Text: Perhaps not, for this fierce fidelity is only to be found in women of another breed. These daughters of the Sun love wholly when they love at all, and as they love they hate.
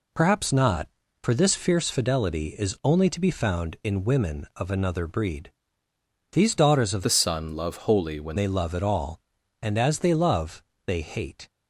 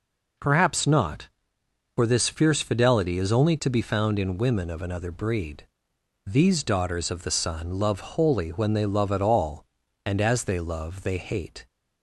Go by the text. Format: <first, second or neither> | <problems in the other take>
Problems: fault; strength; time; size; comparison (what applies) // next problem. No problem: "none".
second | changes voice from "the" to "when"; from 7.0 to 8.3 s; 1.3 s long // pauses between "love" and "they"; slight; at 10.6 s; 0.26 s long